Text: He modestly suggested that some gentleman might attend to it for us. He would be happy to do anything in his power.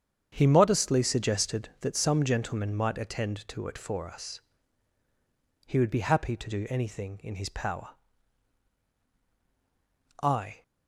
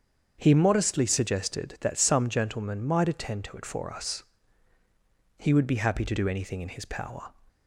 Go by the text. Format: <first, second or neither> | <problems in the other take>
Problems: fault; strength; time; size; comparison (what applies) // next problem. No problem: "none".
second | starts louder than the rest; strong; until 1.3 s; 8 dB; strong in the second // goes on to say "I"; slight; from 10.2 s on; 0.40 s long